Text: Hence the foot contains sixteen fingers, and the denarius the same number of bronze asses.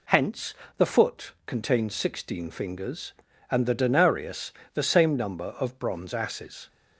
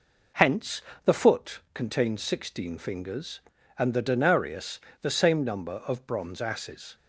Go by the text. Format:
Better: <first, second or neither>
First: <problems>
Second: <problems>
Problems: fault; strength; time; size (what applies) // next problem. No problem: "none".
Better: first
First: pauses between "Hence" and "the"; slight; at 0.5 s; 0.24 s long // pauses between "denarius" and "the"; slight; at 4.5 s; 0.22 s long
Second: starts louder than the rest; noticeable; until 1.8 s; 4.5 dB // pauses between "Hence" and "the"; slight; at 0.7 s; 0.24 s long // pauses between "denarius" and "the"; slight; at 4.7 s; 0.22 s long